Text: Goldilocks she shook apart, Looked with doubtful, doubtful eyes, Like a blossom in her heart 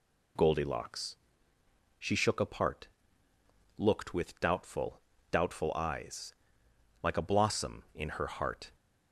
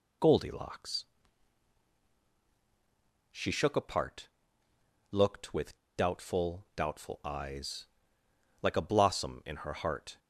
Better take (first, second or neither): first